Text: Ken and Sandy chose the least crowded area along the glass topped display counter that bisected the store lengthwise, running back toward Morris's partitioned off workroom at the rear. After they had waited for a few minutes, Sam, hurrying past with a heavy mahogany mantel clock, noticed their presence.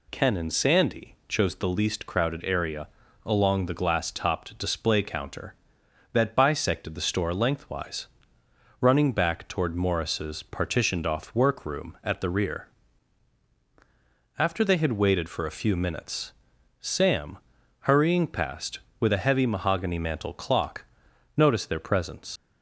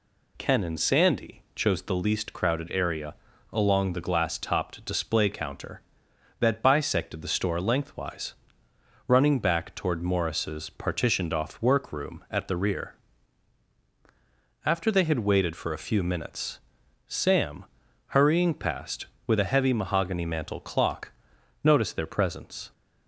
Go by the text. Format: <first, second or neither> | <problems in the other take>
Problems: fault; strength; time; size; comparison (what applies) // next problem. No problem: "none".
second | pauses between "area" and "along"; at 2.8 s; 0.38 s long; also in the second // leaves "presence" unfinished; at 22.3 s; 90 ms